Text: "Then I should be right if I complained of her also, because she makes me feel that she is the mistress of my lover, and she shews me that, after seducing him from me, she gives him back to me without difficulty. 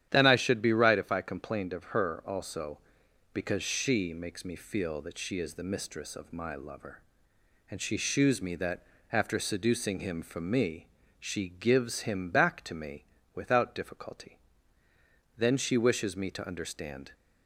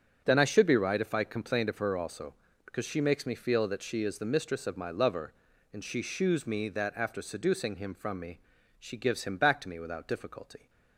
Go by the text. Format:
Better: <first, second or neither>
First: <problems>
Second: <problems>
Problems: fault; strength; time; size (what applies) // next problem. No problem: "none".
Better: second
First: starts louder than the rest; strong; until 1.1 s; 10.5 dB // pauses between "me" and "without"; slight; at 13.0 s; 0.30 s long // goes on to say "Then she wishes me to understand"; strong; from 15.3 s on; 1.7 s long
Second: starts louder than the rest; strong; until 1.2 s; 8 dB